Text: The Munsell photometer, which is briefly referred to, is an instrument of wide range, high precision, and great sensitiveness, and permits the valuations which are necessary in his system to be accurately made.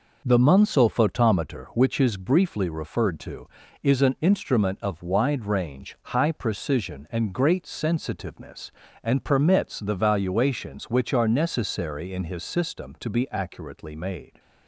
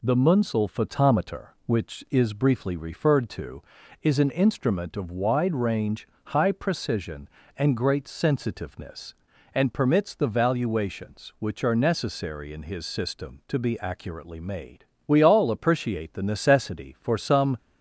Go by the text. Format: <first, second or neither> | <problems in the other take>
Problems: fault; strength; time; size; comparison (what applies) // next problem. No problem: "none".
first | goes on to say "We all appreciate the necessity for some"; strong; from 15.0 s on; 2.5 s long